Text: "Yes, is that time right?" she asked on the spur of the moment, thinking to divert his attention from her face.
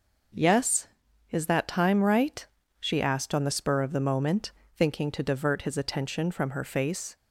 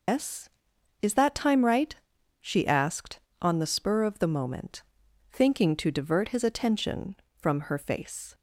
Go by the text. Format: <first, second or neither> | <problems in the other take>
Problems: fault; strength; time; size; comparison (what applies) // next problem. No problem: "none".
first | loses the start of "Yes"; at 0.0 s; 160 ms